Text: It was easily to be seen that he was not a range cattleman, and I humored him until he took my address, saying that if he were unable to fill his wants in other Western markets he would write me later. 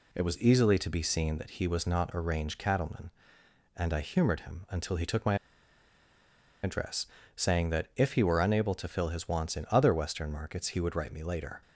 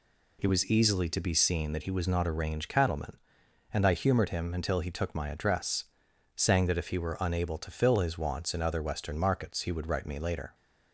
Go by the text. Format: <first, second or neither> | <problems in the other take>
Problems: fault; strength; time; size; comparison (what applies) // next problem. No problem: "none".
second | pauses between "my" and "address"; strong; at 5.3 s; 1.2 s long